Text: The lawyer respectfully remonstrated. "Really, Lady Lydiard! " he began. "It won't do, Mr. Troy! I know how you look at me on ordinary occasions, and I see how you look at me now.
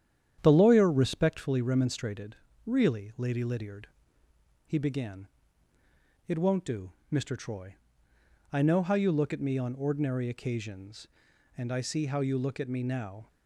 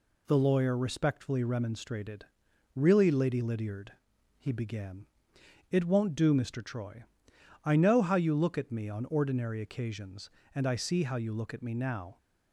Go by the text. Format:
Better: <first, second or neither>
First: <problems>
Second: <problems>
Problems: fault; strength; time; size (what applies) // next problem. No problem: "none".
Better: second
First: starts louder than the rest; strong; until 1.6 s; 9.5 dB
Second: none